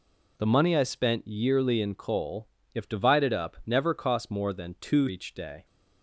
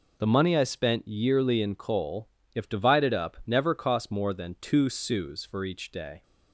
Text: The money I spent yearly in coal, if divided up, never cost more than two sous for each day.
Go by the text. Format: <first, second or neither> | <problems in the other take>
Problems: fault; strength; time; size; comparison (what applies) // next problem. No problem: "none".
second | skips "sous for"; at 5.0 s